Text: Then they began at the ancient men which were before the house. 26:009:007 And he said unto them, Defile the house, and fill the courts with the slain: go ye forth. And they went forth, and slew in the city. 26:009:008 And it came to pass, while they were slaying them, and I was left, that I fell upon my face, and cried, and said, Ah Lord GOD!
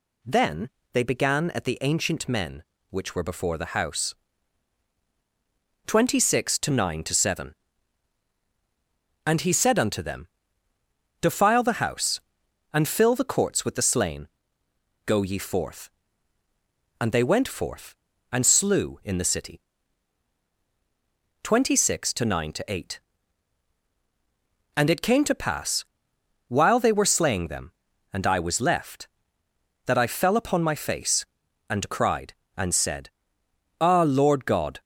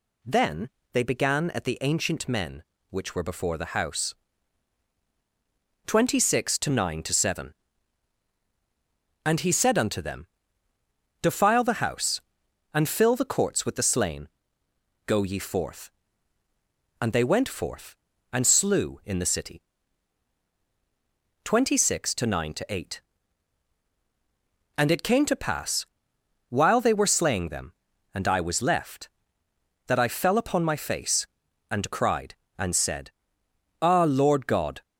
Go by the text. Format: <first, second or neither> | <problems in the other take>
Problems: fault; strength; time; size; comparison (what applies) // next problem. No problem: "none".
neither | pauses between "Then" and "they"; slight; the same in both